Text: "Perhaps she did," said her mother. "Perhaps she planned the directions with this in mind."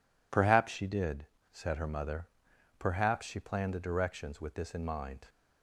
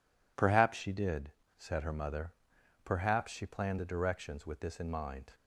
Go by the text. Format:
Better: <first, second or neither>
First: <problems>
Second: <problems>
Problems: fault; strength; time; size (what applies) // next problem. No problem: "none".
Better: neither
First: none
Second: none